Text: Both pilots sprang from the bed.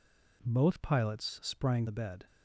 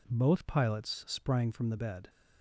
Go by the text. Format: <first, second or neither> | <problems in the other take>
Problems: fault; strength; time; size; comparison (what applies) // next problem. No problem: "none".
second | skips "from"; at 1.8 s